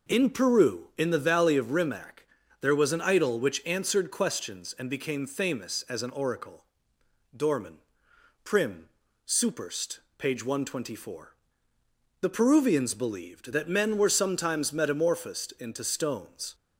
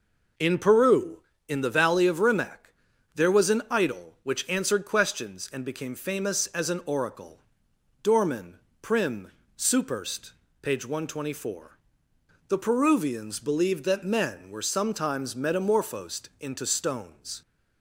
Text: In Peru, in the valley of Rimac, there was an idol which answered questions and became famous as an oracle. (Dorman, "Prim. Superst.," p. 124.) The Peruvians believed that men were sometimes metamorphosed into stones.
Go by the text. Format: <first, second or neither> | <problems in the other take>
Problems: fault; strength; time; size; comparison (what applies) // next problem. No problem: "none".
neither | none